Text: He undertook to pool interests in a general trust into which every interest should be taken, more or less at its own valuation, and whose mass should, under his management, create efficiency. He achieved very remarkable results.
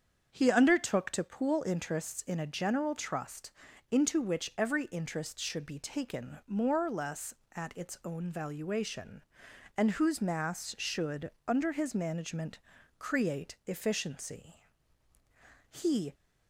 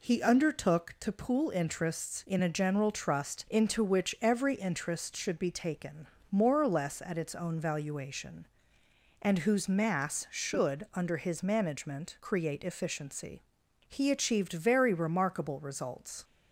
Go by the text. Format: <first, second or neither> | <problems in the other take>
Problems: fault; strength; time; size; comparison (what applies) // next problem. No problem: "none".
second | starts louder than the rest; strong; until 1.3 s; 7.5 dB // pauses between "trust" and "into"; at 3.5 s; 0.38 s long // stops before "achieved very remarkable results"; at 16.1 s